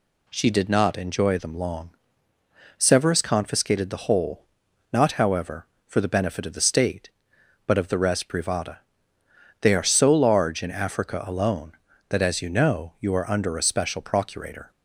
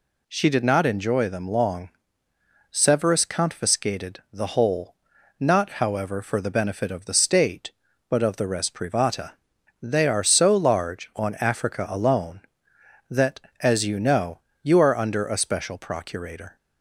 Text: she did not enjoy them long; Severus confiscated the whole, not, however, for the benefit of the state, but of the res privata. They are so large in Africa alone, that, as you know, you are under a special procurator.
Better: first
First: none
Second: says "on" for "in"; at 11.1 s

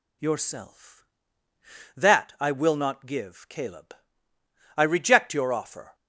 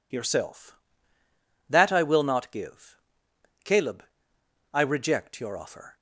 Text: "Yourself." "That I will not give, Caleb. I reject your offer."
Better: neither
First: none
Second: none

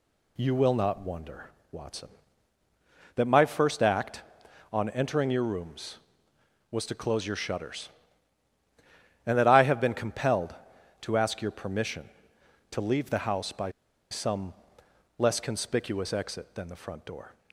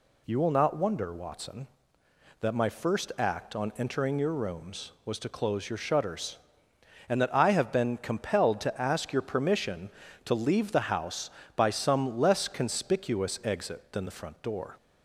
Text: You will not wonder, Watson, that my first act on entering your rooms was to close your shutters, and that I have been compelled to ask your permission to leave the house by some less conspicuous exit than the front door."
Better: second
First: pauses between "by" and "some"; at 13.7 s; 0.40 s long // pauses between "some" and "less"; noticeable; at 14.5 s; 0.66 s long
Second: none

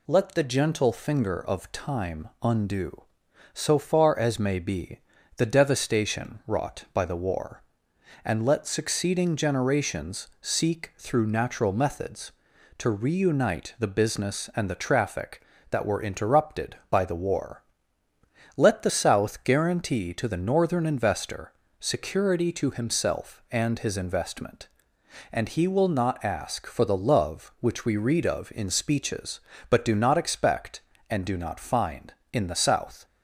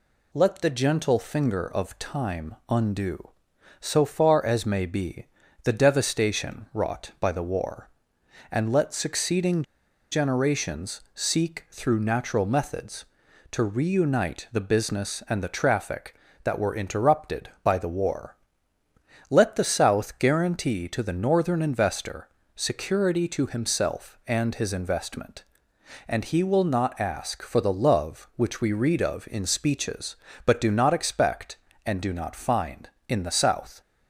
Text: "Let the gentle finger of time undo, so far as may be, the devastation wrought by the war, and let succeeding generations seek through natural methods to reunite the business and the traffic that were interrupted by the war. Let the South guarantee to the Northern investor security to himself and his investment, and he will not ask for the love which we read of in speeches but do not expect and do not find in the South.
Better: first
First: pauses between "investor" and "security"; slight; at 21.5 s; 0.26 s long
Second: pauses between "succeeding" and "generations"; noticeable; at 9.6 s; 0.49 s long // pauses between "investor" and "security"; slight; at 22.2 s; 0.26 s long

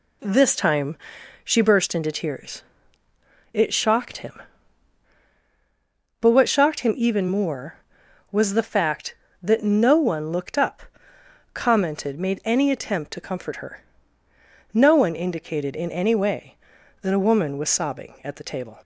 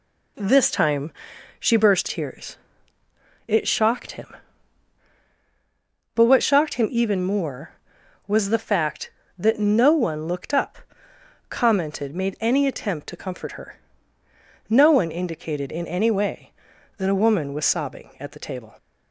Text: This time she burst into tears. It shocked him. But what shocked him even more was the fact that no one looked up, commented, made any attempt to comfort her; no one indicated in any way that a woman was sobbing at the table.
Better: first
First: pauses between "time" and "she"; noticeable; at 0.9 s; 0.46 s long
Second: pauses between "time" and "she"; noticeable; at 1.1 s; 0.46 s long // skips "into"; at 2.0 s

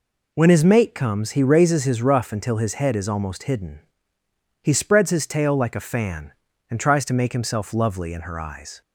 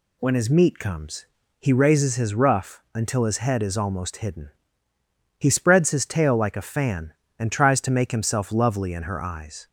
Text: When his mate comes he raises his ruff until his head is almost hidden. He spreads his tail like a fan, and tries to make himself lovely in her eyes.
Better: first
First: none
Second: says "meat" for "mate"; at 0.4 s // pauses between "comes" and "he"; slight; at 1.2 s; 0.36 s long

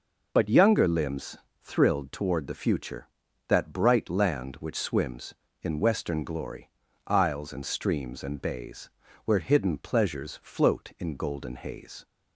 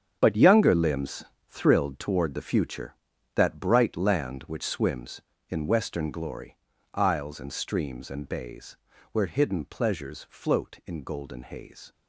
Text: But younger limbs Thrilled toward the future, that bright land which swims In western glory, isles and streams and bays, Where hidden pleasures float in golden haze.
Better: first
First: pauses between "limbs" and "Thrilled"; slight; at 1.3 s; 0.24 s long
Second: gets quieter; strong; throughout; 11.5 dB // pauses between "limbs" and "Thrilled"; slight; at 1.2 s; 0.24 s long

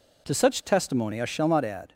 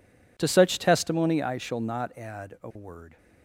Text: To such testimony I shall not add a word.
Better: second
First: stops before "a word"; at 1.9 s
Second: none

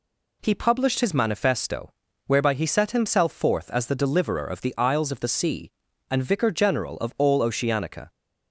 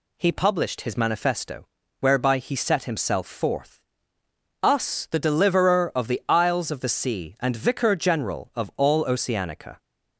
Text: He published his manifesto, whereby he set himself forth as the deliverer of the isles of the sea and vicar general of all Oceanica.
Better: first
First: none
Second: says "us" for "as"; at 4.6 s

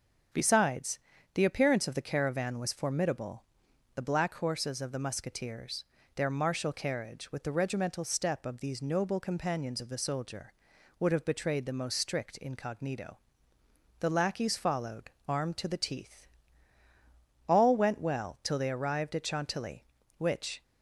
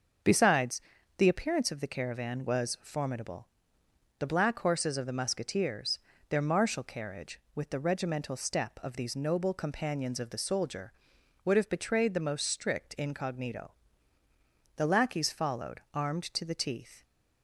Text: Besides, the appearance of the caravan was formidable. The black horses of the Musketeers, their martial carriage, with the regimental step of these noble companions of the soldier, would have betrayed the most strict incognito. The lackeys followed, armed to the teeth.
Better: second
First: starts louder than the rest; strong; until 1.6 s; 7.5 dB // goes on to say "All went well till they arrived at Chantilly which"; strong; from 17.4 s on; 3.1 s long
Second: starts louder than the rest; until 1.6 s; 6.5 dB

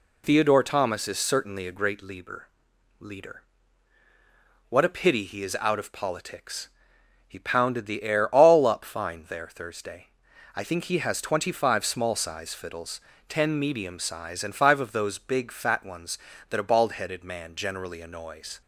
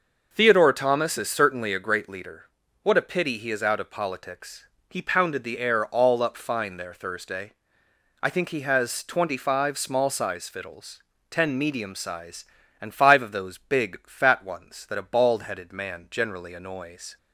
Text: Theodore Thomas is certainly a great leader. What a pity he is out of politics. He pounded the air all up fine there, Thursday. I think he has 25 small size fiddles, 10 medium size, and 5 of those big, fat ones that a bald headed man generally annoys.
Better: second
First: says "leader" twice; at 2.9 s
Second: none

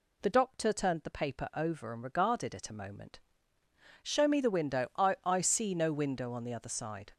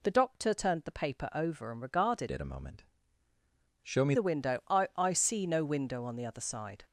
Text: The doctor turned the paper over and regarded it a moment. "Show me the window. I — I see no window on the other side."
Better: first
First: none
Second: changes voice from "it" to "me"; from 2.2 to 4.1 s; 1.9 s long

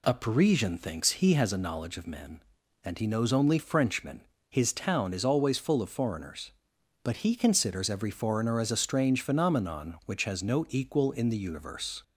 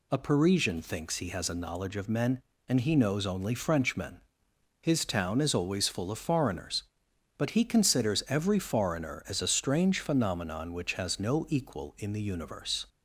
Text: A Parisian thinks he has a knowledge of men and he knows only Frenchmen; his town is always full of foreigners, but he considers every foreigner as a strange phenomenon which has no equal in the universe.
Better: neither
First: none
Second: none

